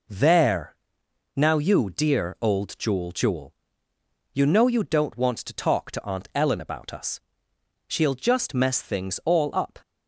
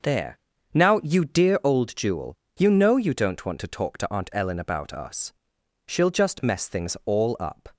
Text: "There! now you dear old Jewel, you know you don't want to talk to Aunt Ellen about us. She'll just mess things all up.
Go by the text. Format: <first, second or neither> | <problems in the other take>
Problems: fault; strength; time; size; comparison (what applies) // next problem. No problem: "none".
second | says "Jewel" twice; at 3.1 s